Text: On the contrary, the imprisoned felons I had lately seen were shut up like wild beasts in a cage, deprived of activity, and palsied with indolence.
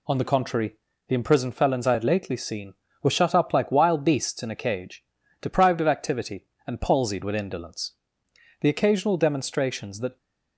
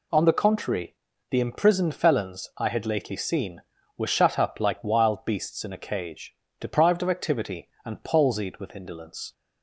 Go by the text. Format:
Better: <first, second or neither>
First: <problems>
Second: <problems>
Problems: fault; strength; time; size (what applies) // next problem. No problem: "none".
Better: second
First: goes on to say "The occasional demonstrations that"; from 8.6 s on; 1.5 s long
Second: none